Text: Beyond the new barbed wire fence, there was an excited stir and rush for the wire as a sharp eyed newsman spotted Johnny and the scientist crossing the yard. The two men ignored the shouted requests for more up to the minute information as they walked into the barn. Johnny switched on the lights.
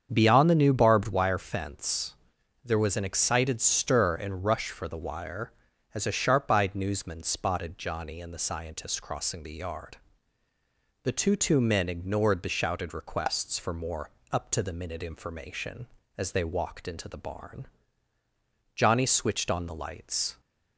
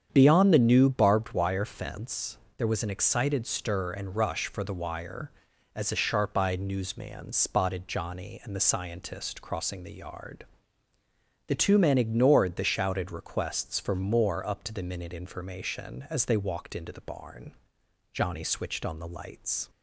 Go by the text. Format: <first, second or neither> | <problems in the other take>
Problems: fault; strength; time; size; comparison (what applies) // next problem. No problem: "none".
second | starts louder than the rest; strong; until 1.1 s; 7.5 dB; strong in the second // says "two" twice; at 11.3 s // pauses between "more" and "up"; slight; at 14.0 s; 0.22 s long